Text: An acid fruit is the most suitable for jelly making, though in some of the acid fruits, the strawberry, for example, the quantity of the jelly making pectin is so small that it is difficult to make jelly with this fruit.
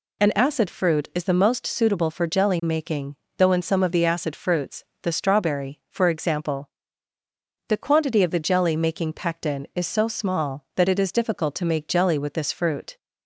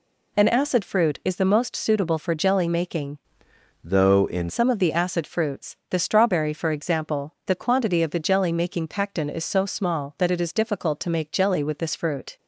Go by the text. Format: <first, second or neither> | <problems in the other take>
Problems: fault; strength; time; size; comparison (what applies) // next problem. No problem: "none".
first | changes voice from "though" to "in"; from 3.8 to 4.4 s; 0.6 s long